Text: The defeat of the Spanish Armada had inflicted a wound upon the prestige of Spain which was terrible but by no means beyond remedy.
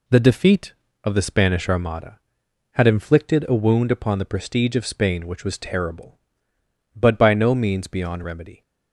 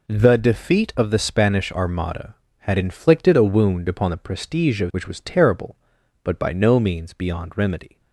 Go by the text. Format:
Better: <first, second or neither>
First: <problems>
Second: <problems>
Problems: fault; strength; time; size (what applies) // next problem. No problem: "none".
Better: first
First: none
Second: skips "Spain"; at 4.9 s